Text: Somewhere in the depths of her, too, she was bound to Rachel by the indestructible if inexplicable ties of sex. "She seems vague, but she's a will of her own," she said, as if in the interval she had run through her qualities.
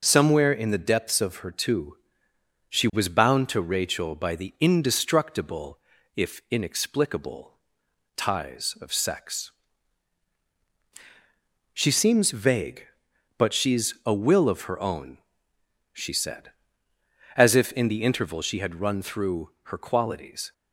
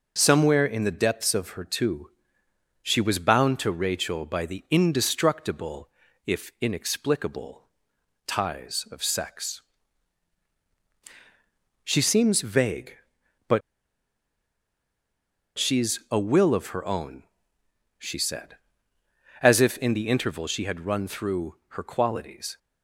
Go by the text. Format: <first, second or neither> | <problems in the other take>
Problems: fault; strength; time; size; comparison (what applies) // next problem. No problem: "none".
first | pauses between "indestructible" and "if"; slight; at 5.8 s; 0.36 s long; slight in the first // pauses between "inexplicable" and "ties"; noticeable; at 7.6 s; 0.60 s long; noticeable in the first // pauses between "but" and "she's"; strong; at 13.6 s; 1.9 s long // pauses between "through" and "her"; slight; at 21.5 s; 0.22 s long; slight in the first